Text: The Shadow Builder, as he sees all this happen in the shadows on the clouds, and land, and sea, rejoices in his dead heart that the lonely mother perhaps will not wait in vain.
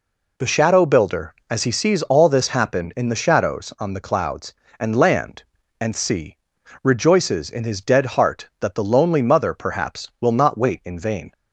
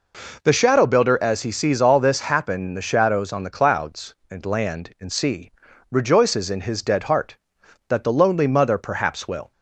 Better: first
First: none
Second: stops before "not wait in vain"; at 9.5 s

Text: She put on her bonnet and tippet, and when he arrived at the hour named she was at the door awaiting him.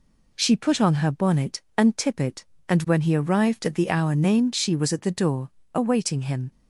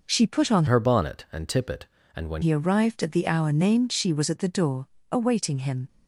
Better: first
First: pauses between "door" and "awaiting"; slight; at 5.5 s; 0.24 s long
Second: changes voice from "her" to "when"; from 0.6 to 2.4 s; 1.8 s long // pauses between "door" and "awaiting"; slight; at 4.8 s; 0.24 s long

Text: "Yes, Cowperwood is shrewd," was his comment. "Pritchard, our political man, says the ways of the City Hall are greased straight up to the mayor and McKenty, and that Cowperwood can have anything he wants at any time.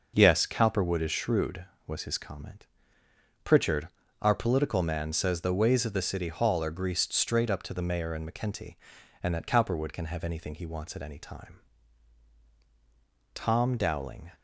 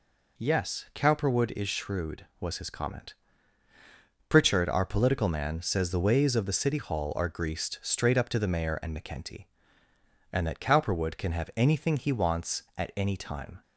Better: second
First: goes on to say "Tom Dowling"; noticeable; from 13.3 s on; 0.96 s long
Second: none

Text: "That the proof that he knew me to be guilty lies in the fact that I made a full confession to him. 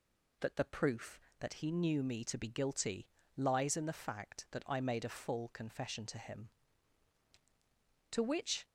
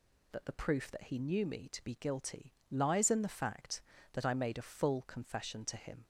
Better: second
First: pauses between "guilty" and "lies"; slight; at 3.0 s; 0.28 s long // goes on to say "To which"; from 8.1 s on; 0.52 s long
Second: pauses between "guilty" and "lies"; slight; at 2.5 s; 0.18 s long

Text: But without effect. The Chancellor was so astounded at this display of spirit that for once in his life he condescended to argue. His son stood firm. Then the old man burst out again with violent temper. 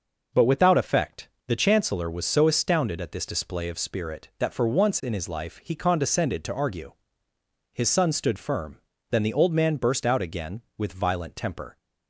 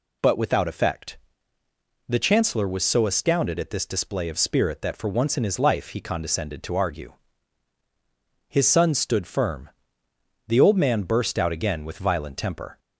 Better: first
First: none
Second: skips "Then"; at 10.0 s

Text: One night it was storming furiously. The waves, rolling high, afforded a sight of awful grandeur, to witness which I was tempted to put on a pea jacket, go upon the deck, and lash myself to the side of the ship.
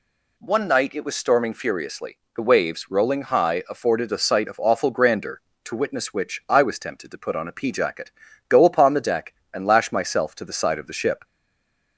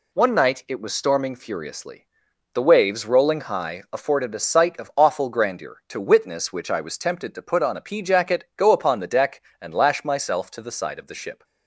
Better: second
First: stays silent after the last word; slight; from 11.2 s on; 0.7 s long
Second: none

